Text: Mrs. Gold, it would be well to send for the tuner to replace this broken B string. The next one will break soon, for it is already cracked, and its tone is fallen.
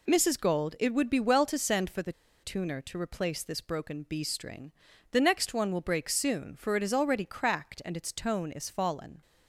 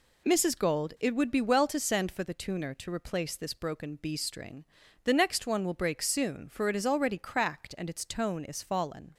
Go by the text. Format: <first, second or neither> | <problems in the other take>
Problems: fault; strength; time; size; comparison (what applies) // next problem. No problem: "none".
second | pauses between "the" and "tuner"; slight; at 2.1 s; 0.30 s long